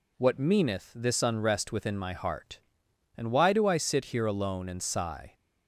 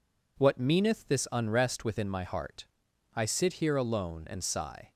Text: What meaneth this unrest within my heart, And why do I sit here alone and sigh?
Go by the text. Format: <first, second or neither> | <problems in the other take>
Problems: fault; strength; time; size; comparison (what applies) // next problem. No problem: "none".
first | skips "And why do"; at 2.9 s